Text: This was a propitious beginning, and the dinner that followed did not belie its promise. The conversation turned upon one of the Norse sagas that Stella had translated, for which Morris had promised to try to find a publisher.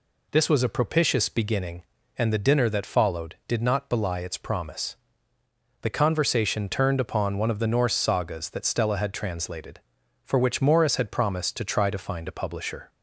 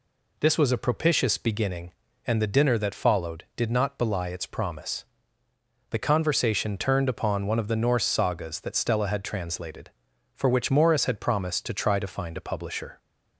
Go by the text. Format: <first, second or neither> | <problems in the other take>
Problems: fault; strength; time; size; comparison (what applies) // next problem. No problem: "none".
neither | none